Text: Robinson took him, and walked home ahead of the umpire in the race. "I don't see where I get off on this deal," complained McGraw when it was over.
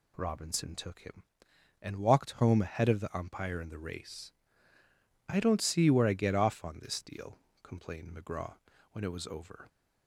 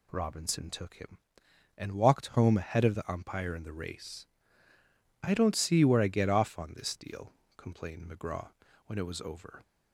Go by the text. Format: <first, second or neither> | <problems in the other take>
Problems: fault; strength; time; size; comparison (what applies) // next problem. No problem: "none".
neither | pauses between "McGraw" and "when"; slight; the same in both